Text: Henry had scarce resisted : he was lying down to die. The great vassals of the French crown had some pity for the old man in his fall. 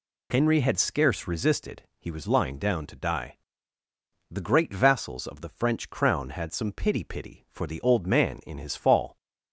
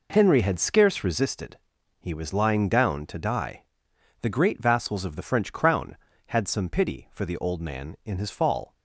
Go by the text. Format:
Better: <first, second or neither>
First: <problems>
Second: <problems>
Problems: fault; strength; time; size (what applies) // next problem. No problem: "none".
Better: second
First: says "pity" twice; at 7.0 s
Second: none